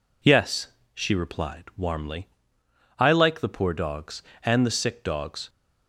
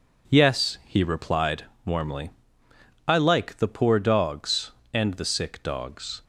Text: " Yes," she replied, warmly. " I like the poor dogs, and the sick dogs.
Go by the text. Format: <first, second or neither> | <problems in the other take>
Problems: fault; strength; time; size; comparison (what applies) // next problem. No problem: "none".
first | says "he" for "she"; at 0.8 s